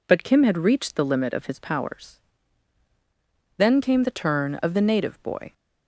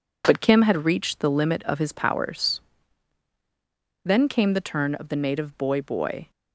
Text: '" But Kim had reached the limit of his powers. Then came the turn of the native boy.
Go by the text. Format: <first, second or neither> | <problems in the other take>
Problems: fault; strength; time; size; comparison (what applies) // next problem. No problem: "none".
first | says "boy" twice; at 5.8 s